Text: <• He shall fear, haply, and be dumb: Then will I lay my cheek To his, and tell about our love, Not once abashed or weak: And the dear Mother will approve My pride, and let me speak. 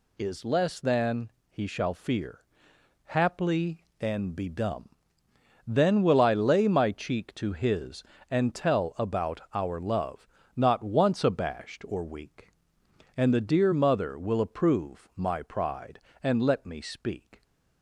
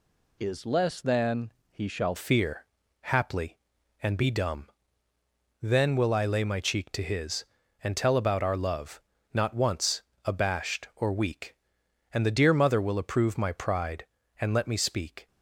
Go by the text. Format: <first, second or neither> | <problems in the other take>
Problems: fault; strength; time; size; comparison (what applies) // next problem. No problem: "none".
first | changes voice at "fear"; from 2.1 s on; 13.1 s long // pauses between "once" and "abashed"; slight; at 10.0 s; 0.24 s long